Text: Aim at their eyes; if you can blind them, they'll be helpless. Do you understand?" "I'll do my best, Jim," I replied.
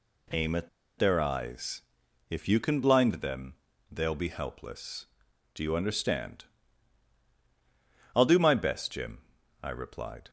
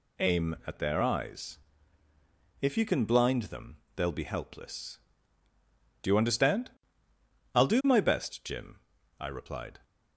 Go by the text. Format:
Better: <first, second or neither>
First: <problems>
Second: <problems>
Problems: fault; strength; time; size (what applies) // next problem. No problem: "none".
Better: second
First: pauses between "at" and "their"; slight; at 0.6 s; 0.29 s long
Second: none